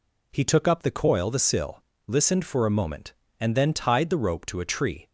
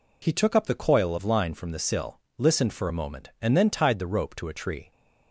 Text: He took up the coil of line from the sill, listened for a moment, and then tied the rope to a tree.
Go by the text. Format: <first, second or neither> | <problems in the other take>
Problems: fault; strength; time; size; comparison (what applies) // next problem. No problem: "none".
second | skips "of line from"; at 1.3 s